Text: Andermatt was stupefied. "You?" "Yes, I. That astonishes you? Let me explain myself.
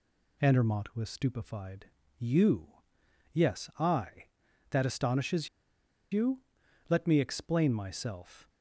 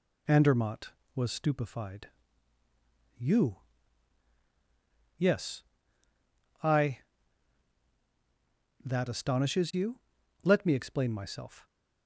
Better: second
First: pauses between "astonishes" and "you"; noticeable; at 5.4 s; 0.63 s long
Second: none

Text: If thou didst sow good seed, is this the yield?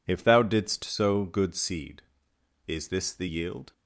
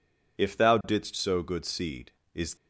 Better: first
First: none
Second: stops before "this the yield"; at 2.5 s

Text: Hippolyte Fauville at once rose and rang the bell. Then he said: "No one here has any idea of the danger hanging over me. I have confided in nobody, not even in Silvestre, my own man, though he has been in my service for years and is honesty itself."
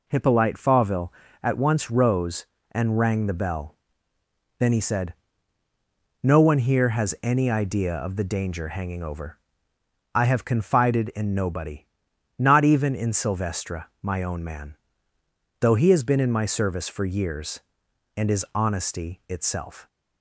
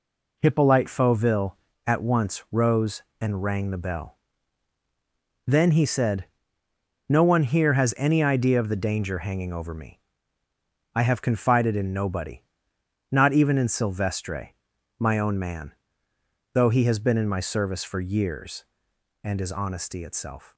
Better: second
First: skips "me"; at 9.7 s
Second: none

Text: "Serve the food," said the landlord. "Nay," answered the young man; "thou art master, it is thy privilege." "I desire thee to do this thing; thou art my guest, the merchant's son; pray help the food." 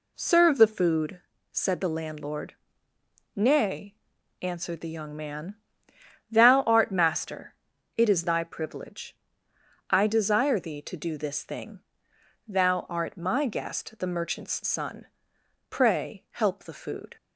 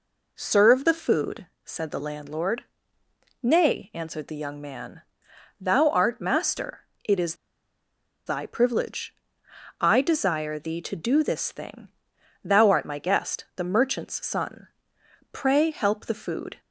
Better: first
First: none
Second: pauses between "is" and "thy"; noticeable; at 7.3 s; 0.90 s long

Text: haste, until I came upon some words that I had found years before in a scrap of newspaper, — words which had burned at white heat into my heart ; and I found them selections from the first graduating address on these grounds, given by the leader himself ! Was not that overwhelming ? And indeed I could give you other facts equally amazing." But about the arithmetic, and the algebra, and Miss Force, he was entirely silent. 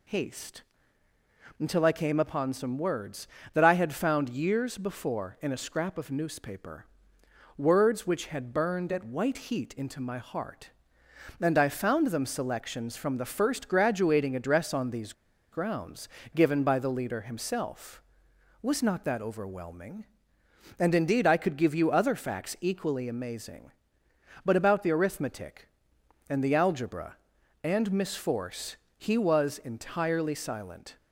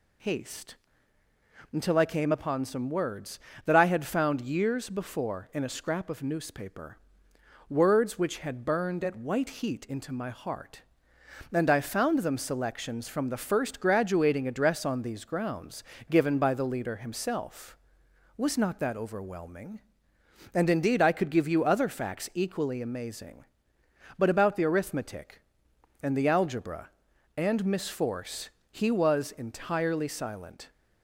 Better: second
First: pauses between "these" and "grounds"; at 15.1 s; 0.39 s long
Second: none

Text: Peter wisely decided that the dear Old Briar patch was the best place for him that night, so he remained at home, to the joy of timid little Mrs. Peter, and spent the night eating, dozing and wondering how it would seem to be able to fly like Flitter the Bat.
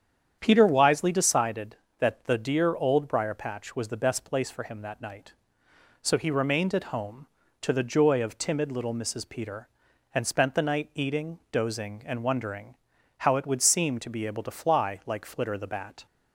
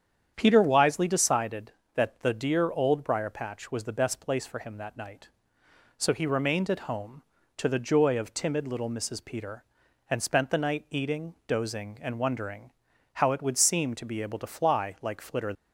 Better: first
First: starts louder than the rest; strong; until 1.4 s; 8.5 dB // pauses between "wondering" and "how"; at 12.7 s; 0.42 s long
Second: starts louder than the rest; strong; until 1.3 s; 8.5 dB // pauses between "wondering" and "how"; at 12.7 s; 0.42 s long // stops before "the Bat"; at 15.5 s

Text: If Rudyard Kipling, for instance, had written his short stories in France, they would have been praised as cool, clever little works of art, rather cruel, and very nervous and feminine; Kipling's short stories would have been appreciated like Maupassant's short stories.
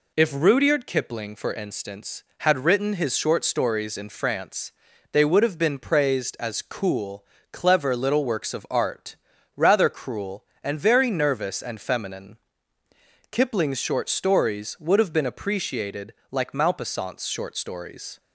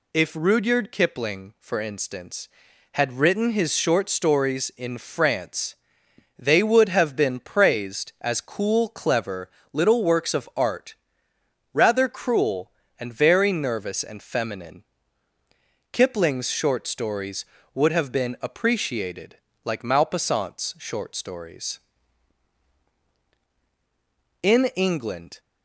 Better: first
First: pauses between "appreciated" and "like"; slight; at 16.1 s; 0.16 s long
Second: pauses between "clever" and "little"; slight; at 9.4 s; 0.22 s long // pauses between "appreciated" and "like"; slight; at 19.3 s; 0.26 s long // goes on to say "In England"; noticeable; from 24.4 s on; 0.96 s long

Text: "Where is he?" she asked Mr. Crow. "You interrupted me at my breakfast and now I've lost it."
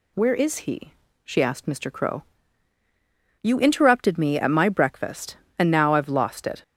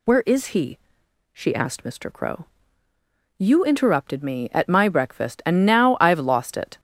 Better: first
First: none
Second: gets louder; noticeable; throughout; 5.5 dB

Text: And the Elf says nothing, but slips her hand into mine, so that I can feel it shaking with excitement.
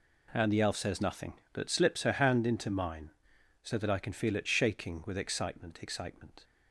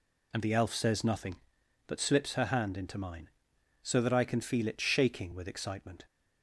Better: second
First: says "excitement" twice; at 5.8 s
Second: none

